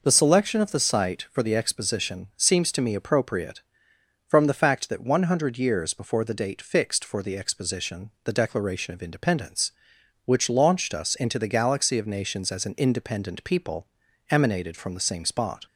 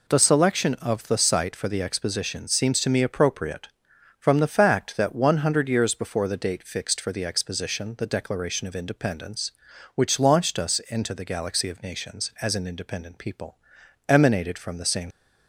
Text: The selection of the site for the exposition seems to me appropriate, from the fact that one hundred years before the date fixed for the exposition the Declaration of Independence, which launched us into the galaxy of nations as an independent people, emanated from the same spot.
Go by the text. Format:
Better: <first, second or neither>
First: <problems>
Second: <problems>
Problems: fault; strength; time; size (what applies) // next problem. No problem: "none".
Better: first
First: none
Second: stops before "spot"; at 15.1 s